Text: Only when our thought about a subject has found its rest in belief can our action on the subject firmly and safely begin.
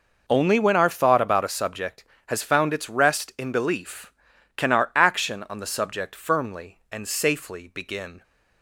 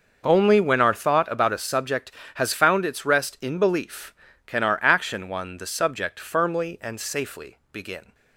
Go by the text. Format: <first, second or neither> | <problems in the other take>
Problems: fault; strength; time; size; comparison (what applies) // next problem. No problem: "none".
first | says "one" for "on"; at 5.2 s